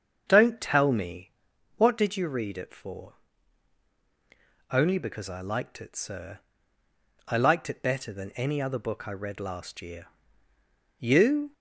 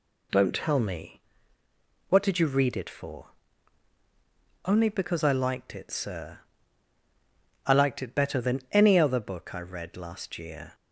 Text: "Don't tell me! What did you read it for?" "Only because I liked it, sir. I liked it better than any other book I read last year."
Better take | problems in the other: second | starts louder than the rest; until 1.2 s; 7 dB // goes on to say "You"; from 10.9 s on; 0.54 s long

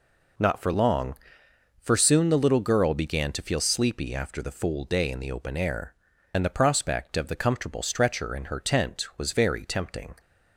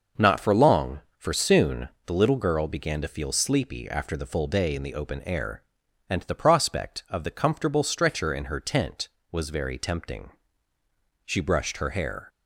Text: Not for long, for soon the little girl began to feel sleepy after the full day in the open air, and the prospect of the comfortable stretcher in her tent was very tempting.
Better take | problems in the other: first | pauses between "soon" and "the"; slight; at 1.8 s; 0.16 s long // goes on to say "She brushed her hair"; noticeable; from 11.2 s on; 1.0 s long

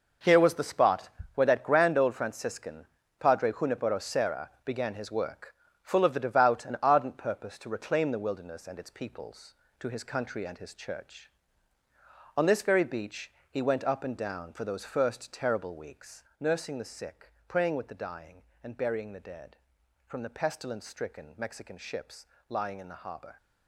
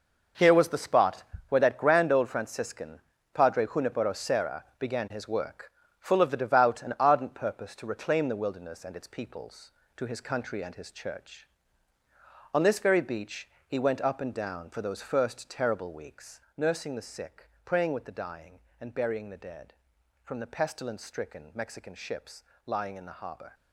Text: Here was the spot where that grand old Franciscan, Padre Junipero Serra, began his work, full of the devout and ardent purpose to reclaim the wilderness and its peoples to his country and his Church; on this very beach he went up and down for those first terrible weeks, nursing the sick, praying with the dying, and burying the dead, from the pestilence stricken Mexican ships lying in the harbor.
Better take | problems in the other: neither | pauses between "spot" and "where"; slight; the same in both // pauses between "beach" and "he"; slight; the same in both // pauses between "ships" and "lying"; slight; the same in both

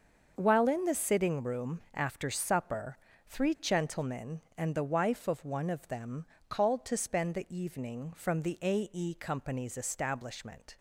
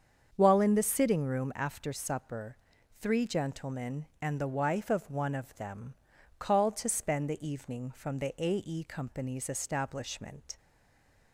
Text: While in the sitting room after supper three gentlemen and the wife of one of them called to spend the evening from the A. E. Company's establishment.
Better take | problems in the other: first | starts louder than the rest; strong; until 1.3 s; 7 dB; also in the first // pauses between "supper" and "three"; at 2.5 s; 0.42 s long; slight in the first // pauses between "them" and "called"; at 5.9 s; 0.44 s long; slight in the first // stays silent after the last word; slight; from 10.5 s on; 0.8 s long

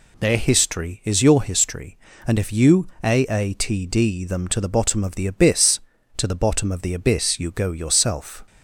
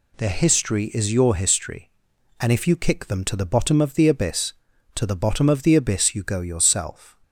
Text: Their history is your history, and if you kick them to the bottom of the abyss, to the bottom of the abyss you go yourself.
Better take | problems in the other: second | says "aatd" for "kick"; at 3.0 s

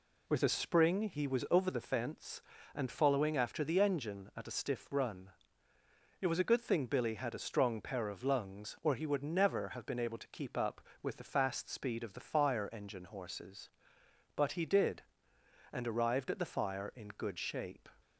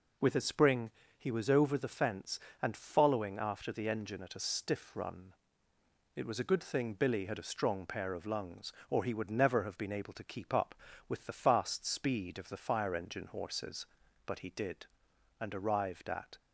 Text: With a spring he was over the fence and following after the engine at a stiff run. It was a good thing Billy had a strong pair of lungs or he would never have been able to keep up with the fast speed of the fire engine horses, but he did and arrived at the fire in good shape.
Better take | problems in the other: first | pauses between "spring" and "he"; slight; at 0.8 s; 0.28 s long // stops before "the fire in good shape"; at 16.3 s

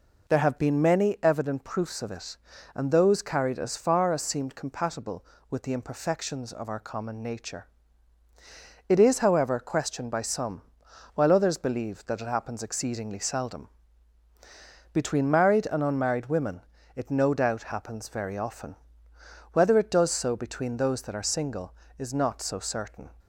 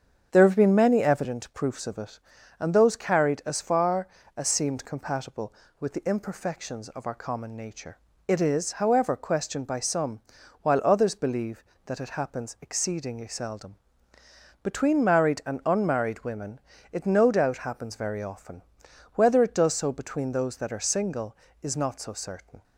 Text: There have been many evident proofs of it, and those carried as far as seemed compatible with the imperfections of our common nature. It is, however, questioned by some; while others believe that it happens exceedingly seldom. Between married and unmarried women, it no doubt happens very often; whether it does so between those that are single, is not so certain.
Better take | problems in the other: first | starts louder than the rest; strong; until 1.3 s; 8 dB

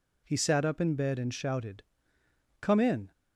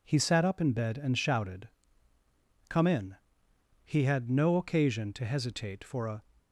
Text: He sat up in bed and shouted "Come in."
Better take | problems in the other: first | pauses between "shouted" and "Come"; at 1.6 s; 1.0 s long; noticeable in the first // goes on to say "He had no occasion to hesitate for a"; strong; from 3.8 s on; 2.3 s long

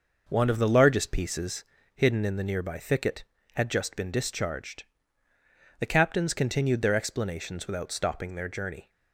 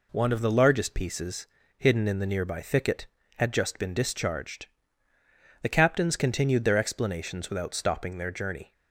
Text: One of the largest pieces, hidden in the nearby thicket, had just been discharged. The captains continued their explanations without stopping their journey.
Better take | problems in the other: second | starts louder than the rest; noticeable; until 2.0 s; 6 dB

